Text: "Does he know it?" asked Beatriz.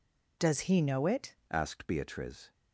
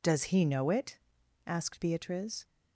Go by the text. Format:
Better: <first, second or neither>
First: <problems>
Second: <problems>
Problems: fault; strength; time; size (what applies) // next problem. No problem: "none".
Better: second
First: changes voice at "asked"; from 1.5 s on; 1.0 s long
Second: none